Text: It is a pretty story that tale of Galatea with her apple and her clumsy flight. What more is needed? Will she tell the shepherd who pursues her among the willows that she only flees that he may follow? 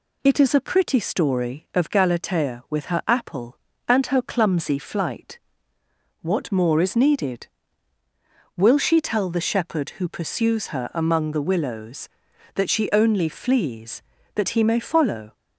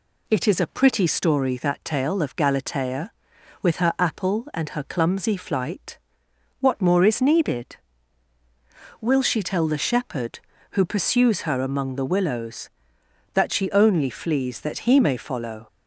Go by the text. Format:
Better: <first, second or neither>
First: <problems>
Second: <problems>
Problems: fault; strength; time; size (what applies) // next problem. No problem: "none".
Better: second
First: skips "that tale"; at 1.6 s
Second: none